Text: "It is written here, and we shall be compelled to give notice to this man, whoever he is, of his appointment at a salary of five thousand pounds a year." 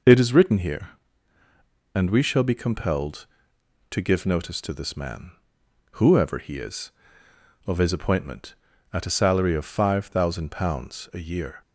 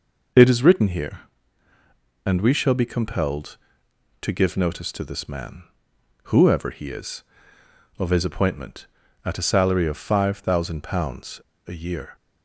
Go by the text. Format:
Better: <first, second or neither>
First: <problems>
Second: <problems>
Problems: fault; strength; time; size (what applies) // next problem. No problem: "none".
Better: first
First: none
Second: pauses between "pounds" and "a"; slight; at 11.3 s; 0.28 s long